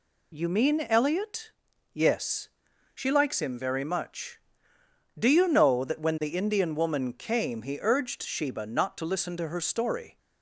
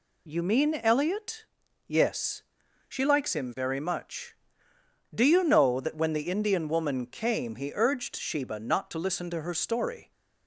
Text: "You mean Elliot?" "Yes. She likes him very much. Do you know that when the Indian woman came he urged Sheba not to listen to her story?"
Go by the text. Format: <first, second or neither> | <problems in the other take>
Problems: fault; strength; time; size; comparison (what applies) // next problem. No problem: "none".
neither | none